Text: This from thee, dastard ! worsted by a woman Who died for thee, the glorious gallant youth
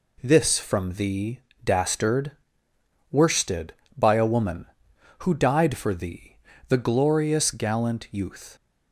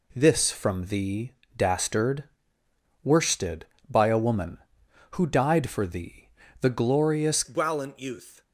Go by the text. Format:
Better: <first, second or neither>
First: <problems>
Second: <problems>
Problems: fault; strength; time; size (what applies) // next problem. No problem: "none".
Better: first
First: none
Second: changes voice at "gallant"; from 7.4 s on; 1.0 s long